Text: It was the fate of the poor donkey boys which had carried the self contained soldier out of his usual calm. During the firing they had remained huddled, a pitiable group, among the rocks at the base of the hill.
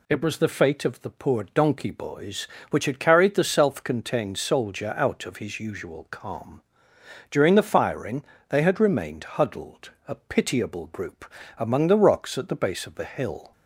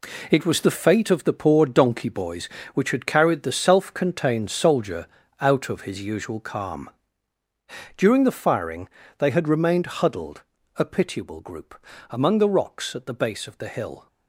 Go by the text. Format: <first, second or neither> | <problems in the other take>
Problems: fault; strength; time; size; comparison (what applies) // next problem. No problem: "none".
first | gets quieter; strong; throughout; 8.5 dB // pauses between "soldier" and "out"; slight; at 5.0 s; 0.32 s long // pauses between "firing" and "they"; slight; at 8.8 s; 0.30 s long; slight in the first